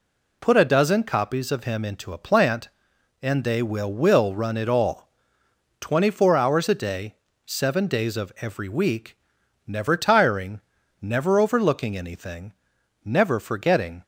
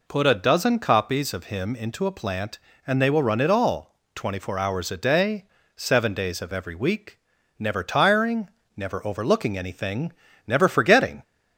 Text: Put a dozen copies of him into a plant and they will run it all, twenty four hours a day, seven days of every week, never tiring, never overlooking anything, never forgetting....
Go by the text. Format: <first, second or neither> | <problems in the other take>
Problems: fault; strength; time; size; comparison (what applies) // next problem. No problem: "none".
second | says "will" twice; at 3.9 s